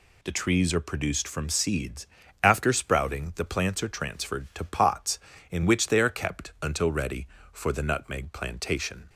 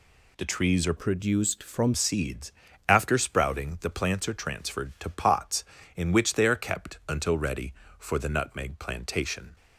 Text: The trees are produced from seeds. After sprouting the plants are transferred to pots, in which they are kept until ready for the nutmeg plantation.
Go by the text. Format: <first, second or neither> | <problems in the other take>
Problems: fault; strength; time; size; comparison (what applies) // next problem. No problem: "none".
first | changes voice from "produced" to "from"; from 0.9 to 1.9 s; 1.0 s long